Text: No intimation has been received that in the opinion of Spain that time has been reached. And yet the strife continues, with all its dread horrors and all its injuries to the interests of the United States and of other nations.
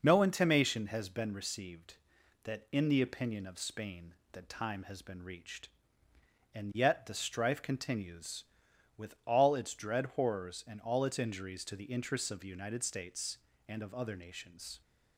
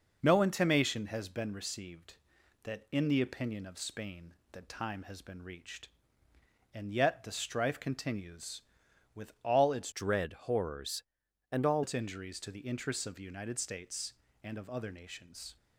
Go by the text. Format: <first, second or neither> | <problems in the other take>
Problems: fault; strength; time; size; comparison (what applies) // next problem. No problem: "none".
first | changes voice from "dread" to "all"; from 9.9 to 11.8 s; 1.9 s long